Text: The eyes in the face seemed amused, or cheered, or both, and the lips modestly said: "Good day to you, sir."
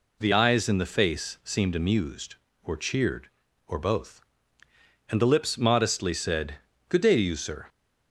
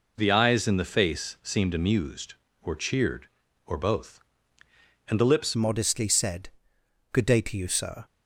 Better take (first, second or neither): first